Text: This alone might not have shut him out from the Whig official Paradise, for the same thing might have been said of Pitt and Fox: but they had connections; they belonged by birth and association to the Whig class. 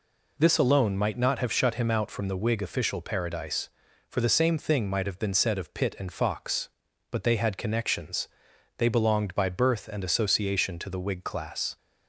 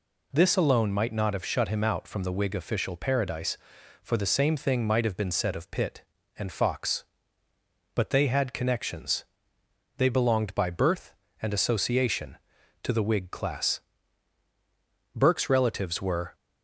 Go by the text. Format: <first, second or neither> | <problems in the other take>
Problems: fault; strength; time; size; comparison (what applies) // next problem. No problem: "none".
first | goes on to say "Burke's relatives were"; noticeable; from 15.1 s on; 1.2 s long